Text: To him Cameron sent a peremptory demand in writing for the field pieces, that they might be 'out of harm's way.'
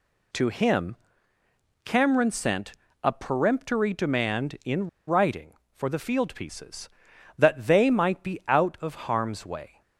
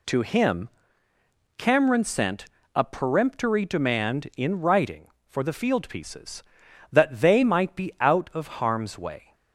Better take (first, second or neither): second